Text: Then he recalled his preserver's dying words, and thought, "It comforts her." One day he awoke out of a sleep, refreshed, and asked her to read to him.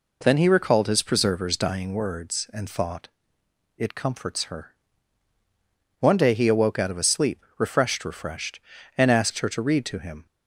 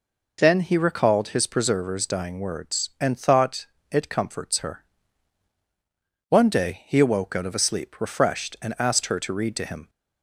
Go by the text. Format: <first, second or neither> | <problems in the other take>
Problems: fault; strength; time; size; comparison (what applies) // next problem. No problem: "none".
second | says "refreshed" twice; at 8.0 s